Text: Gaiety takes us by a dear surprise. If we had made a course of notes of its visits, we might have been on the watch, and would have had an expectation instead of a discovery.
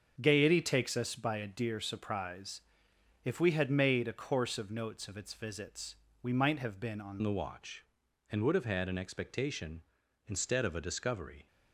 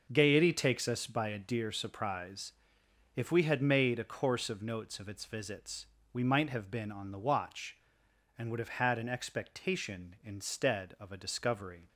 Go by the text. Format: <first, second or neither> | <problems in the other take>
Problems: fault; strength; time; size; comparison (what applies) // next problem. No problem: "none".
second | starts louder than the rest; until 1.2 s; 7 dB; also in the second // changes voice at "the"; from 7.2 s on; 4.2 s long